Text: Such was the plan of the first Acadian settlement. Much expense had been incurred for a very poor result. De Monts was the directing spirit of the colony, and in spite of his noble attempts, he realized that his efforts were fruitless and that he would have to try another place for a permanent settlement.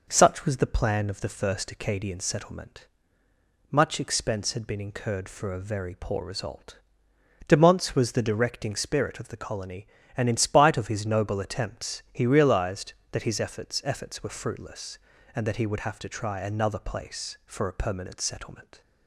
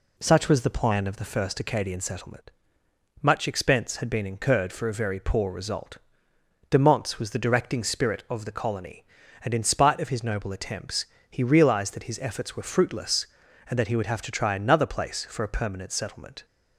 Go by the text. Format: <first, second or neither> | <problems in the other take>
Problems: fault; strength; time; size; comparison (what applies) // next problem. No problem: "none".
second | says "efforts" twice; at 13.8 s